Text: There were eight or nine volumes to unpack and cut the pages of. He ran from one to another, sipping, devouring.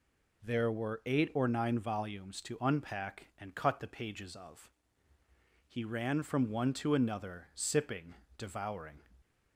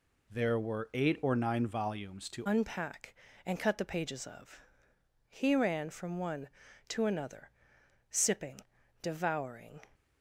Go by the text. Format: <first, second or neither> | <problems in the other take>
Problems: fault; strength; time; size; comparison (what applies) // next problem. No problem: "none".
first | changes voice at "unpack"; from 2.4 s on; 7.4 s long